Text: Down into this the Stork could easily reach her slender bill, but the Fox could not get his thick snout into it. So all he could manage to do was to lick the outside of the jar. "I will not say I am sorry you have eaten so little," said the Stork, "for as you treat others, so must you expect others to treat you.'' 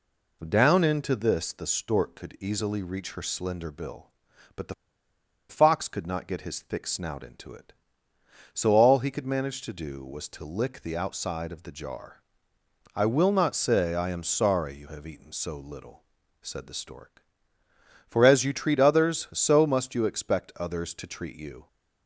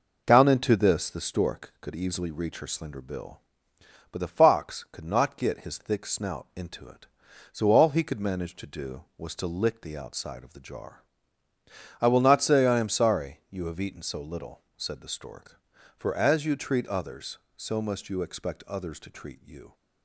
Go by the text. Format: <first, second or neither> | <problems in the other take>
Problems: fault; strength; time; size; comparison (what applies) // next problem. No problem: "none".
second | pauses between "the" and "Fox"; noticeable; at 4.7 s; 0.75 s long